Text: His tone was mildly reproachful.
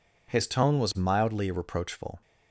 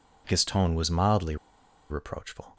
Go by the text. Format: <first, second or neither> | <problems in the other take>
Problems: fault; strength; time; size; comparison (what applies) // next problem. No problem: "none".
first | pauses between "mildly" and "reproachful"; noticeable; at 1.3 s; 0.54 s long